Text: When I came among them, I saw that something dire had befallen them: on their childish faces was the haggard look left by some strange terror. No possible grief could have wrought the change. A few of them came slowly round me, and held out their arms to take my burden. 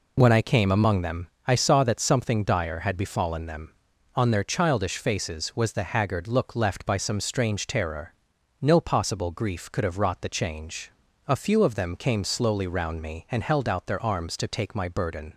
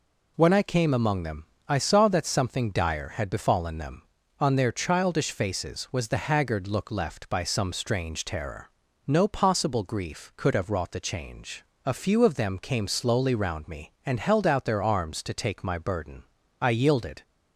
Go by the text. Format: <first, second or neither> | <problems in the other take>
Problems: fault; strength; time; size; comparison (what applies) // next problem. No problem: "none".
first | goes on to say "I yielded"; noticeable; from 16.6 s on; 0.62 s long